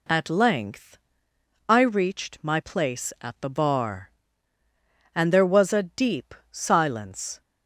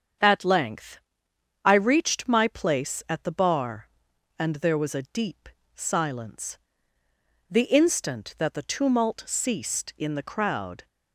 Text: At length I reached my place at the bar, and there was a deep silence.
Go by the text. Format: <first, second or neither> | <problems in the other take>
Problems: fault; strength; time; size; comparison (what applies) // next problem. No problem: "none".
first | starts louder than the rest; strong; until 1.8 s; 7.5 dB // pauses between "length" and "I"; noticeable; at 0.9 s; 0.64 s long; noticeable in the first // pauses between "deep" and "silence"; slight; at 5.4 s; 0.26 s long; slight in the first // goes on to say "The instant that the tumult ceased in the crowd"; strong; from 7.5 s on; 3.3 s long